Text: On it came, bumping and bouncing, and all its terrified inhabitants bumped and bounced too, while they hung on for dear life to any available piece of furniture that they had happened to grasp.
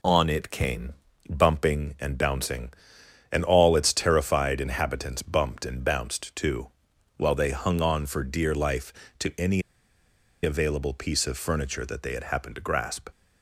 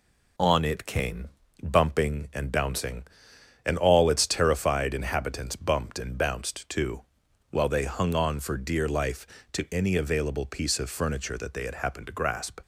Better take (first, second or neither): second